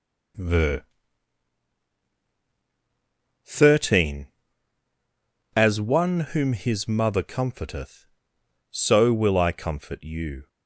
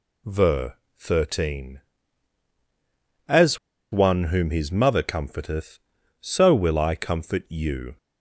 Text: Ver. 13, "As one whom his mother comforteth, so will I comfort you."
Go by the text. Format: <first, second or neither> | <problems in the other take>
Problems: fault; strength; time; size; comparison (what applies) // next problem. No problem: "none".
first | pauses between "As" and "one"; slight; at 3.5 s; 0.34 s long